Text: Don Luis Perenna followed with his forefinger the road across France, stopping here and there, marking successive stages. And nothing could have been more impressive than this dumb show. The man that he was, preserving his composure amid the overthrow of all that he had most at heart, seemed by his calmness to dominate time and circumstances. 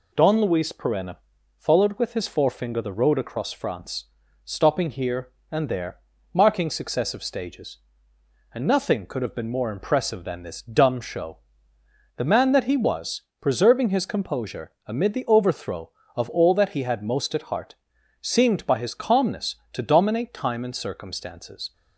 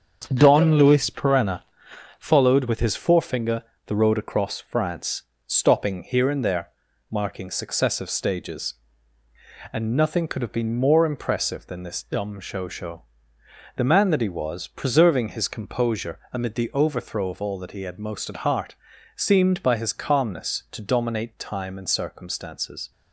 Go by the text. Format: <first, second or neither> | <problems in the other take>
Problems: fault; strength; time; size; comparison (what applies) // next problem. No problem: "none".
first | starts louder than the rest; strong; until 1.3 s; 7.5 dB // pauses between "Perenna" and "followed"; noticeable; at 1.6 s; 0.56 s long; also in the first // pauses between "forefinger" and "the"; slight; at 3.6 s; 0.24 s long // says "show" twice; at 12.6 s